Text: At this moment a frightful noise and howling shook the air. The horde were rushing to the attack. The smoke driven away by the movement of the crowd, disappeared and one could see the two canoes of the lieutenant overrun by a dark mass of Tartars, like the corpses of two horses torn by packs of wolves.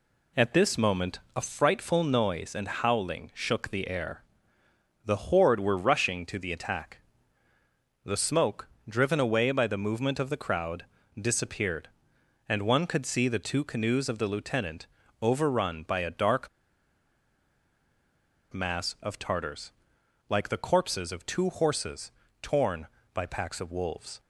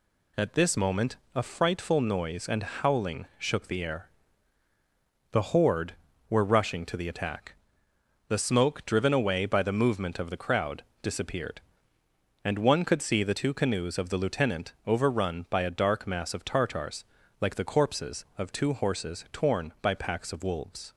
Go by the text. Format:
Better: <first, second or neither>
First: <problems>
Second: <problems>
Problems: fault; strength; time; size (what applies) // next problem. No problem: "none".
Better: second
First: pauses between "moment" and "a"; slight; at 1.1 s; 0.16 s long // pauses between "smoke" and "driven"; slight; at 8.6 s; 0.22 s long // pauses between "lieutenant" and "overrun"; slight; at 14.8 s; 0.34 s long // pauses between "dark" and "mass"; strong; at 16.4 s; 2.0 s long // pauses between "horses" and "torn"; slight; at 22.1 s; 0.30 s long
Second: pauses between "moment" and "a"; slight; at 1.1 s; 0.20 s long